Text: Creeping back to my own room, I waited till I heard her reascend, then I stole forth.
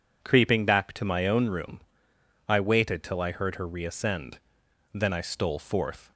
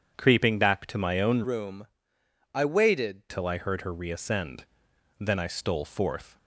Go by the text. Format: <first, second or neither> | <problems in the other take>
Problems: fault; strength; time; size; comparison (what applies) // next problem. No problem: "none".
first | changes voice from "room" to "waited"; from 1.4 to 3.2 s; 1.8 s long